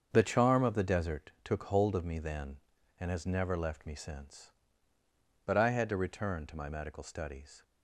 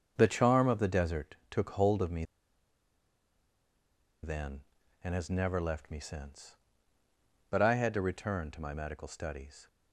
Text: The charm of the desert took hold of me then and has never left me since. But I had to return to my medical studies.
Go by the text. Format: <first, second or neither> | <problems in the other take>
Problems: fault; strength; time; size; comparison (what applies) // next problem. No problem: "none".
first | starts louder than the rest; until 1.1 s; 7 dB; also in the first // pauses between "me" and "then"; strong; at 2.2 s; 1.9 s long